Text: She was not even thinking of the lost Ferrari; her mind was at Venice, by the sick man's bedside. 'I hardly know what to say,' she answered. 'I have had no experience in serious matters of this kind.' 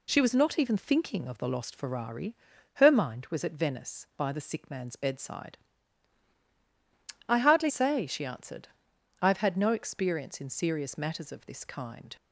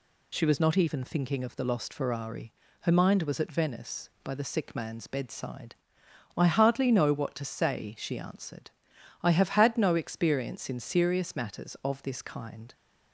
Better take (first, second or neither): second